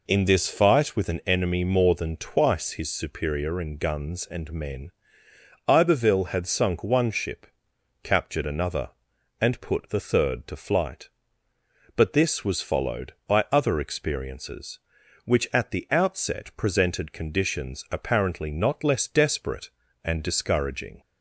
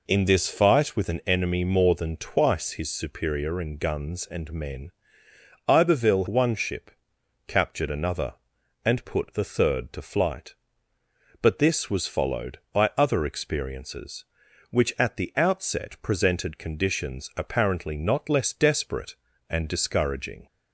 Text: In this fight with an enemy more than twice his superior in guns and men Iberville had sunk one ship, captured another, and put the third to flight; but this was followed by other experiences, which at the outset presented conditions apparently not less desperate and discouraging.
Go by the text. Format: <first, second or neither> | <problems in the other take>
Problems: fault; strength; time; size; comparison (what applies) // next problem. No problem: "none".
first | pauses between "men" and "Iberville"; noticeable; at 4.9 s; 0.76 s long; noticeable in the first // skips "had sunk"; at 6.2 s